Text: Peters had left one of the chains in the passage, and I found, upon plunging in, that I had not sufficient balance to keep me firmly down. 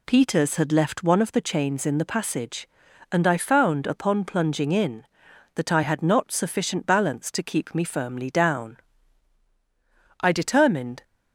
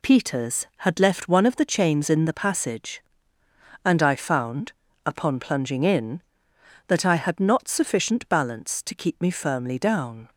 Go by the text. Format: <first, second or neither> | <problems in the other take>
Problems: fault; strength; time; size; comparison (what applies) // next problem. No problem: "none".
second | goes on to say "I determined"; noticeable; from 10.2 s on; 0.82 s long